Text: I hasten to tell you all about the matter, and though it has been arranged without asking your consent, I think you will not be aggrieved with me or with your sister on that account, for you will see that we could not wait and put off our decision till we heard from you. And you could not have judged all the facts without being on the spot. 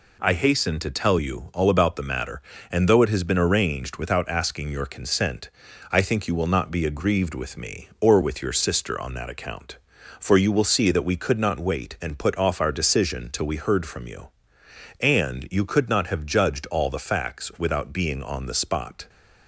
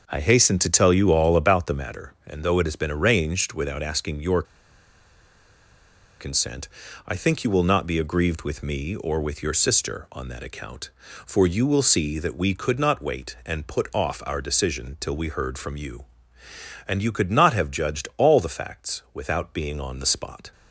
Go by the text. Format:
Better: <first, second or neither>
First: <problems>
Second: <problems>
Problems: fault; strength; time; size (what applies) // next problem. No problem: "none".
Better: first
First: none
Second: starts louder than the rest; noticeable; until 1.0 s; 6 dB // pauses between "your" and "consent"; strong; at 4.4 s; 1.7 s long